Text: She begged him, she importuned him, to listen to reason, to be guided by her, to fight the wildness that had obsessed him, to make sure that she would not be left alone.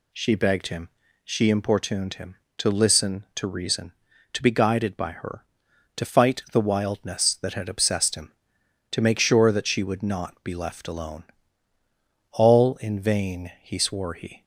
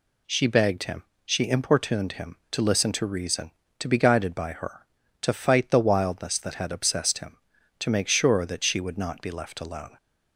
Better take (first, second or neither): second